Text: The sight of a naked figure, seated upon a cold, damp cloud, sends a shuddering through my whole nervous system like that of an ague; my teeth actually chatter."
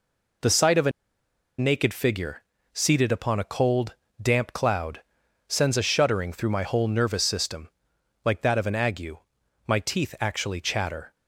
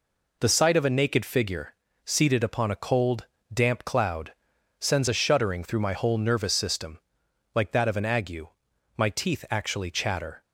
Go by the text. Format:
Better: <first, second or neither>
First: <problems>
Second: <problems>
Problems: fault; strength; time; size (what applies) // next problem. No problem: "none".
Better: second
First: pauses between "a" and "naked"; noticeable; at 0.9 s; 0.67 s long // pauses between "system" and "like"; noticeable; at 7.6 s; 0.56 s long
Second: pauses between "system" and "like"; noticeable; at 6.9 s; 0.56 s long